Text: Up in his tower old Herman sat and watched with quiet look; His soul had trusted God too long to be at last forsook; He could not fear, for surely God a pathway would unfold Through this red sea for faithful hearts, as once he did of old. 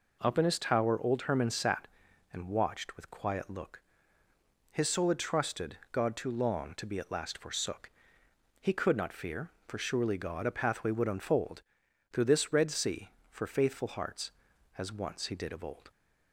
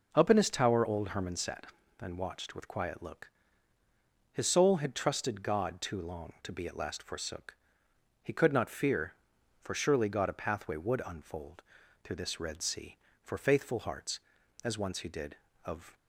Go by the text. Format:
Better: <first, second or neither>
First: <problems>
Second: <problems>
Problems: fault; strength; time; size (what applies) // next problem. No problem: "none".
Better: first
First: pauses between "unfold" and "Through"; noticeable; at 11.6 s; 0.50 s long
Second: pauses between "unfold" and "Through"; at 11.6 s; 0.42 s long // stops before "old"; at 15.9 s